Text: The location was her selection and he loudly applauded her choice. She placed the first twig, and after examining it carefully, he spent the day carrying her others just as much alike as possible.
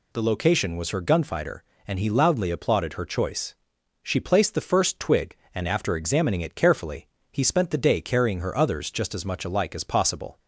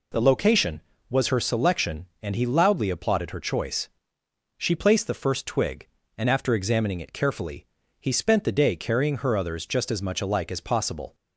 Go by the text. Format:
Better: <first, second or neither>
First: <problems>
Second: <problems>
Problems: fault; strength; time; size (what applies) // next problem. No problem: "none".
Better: second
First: says "gunfighter" for "selection"; at 1.0 s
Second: none